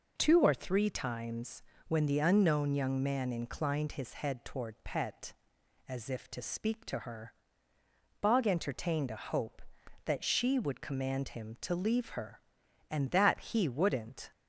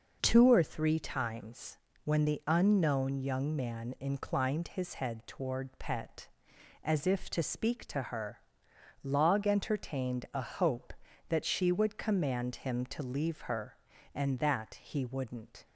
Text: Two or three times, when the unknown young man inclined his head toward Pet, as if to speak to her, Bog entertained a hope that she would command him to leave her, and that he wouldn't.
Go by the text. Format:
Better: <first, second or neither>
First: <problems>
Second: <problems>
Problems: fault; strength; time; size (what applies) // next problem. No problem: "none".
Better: first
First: none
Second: says "Log" for "Bog"; at 9.0 s